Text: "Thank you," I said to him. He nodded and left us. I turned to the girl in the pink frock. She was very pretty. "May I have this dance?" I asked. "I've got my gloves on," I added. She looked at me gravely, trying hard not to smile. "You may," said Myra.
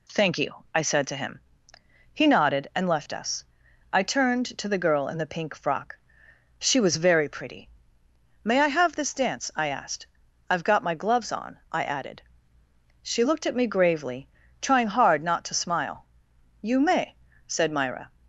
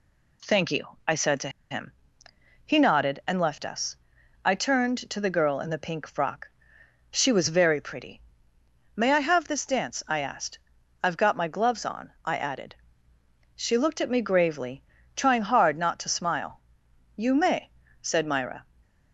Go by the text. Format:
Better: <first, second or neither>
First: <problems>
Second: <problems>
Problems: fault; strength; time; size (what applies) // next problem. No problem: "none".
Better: first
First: none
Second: pauses between "to" and "him"; slight; at 1.4 s; 0.20 s long